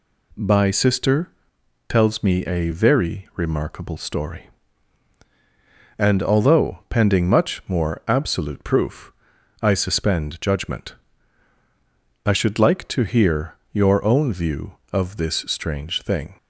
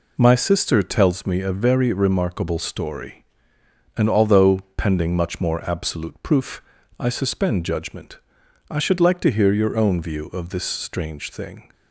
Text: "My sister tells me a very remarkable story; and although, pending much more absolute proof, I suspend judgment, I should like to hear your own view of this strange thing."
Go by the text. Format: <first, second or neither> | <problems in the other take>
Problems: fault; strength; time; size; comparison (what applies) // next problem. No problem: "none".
second | says "By" for "My"; at 0.3 s // pauses between "sister" and "tells"; noticeable; at 1.2 s; 0.60 s long // pauses between "hear" and "your"; slight; at 13.5 s; 0.18 s long